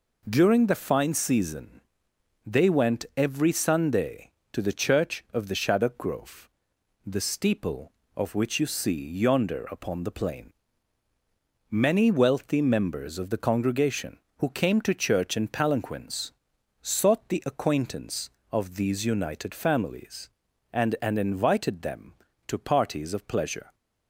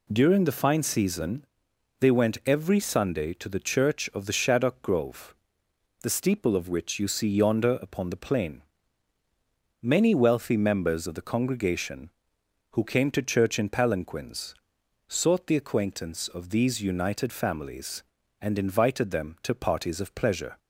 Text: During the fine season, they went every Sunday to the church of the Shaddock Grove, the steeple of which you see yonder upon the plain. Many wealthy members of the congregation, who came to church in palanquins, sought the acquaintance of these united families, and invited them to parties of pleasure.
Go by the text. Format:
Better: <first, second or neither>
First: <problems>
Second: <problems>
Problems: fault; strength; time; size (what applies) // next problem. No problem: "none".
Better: second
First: says "and" twice; at 21.0 s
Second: none